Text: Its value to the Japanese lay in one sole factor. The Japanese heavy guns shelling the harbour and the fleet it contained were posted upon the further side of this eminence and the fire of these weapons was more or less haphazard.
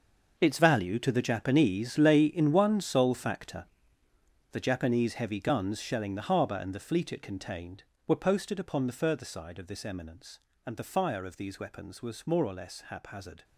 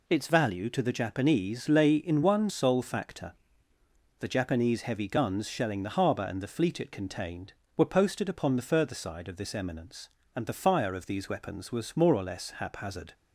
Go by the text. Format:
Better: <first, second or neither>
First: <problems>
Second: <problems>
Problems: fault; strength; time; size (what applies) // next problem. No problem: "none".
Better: second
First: gets quieter; strong; throughout; 14 dB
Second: none